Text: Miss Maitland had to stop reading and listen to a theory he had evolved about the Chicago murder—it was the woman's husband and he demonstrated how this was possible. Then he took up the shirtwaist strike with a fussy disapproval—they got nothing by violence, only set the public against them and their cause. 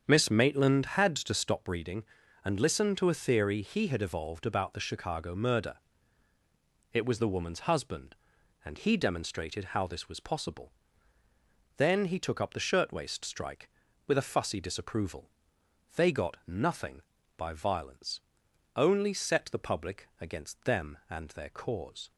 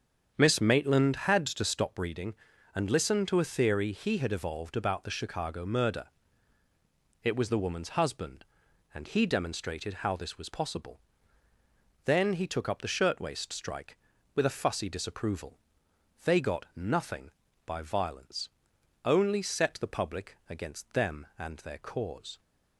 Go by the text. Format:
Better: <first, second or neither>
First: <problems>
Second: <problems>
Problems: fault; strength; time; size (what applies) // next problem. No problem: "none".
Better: neither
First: starts louder than the rest; strong; until 1.0 s; 7.5 dB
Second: starts louder than the rest; strong; until 1.3 s; 7.5 dB